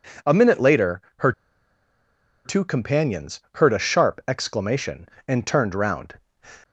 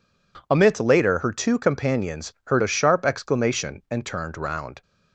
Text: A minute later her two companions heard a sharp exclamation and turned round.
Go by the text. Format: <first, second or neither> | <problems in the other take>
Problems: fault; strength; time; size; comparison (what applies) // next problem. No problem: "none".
second | pauses between "later" and "her"; slight; at 1.0 s; 0.20 s long // pauses between "her" and "two"; at 1.3 s; 1.1 s long